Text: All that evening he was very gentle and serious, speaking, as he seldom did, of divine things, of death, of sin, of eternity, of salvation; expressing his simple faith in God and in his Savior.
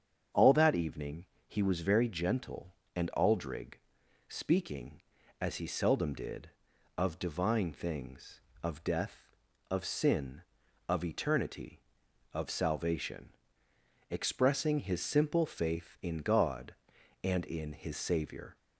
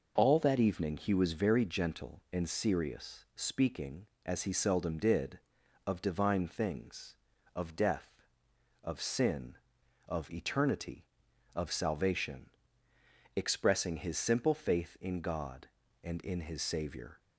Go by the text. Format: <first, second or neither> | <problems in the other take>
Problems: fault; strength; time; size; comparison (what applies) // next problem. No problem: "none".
second | starts louder than the rest; strong; until 1.5 s; 8 dB // pauses between "evening" and "he"; slight; at 1.2 s; 0.20 s long // says "aldrig" for "serious"; at 3.1 s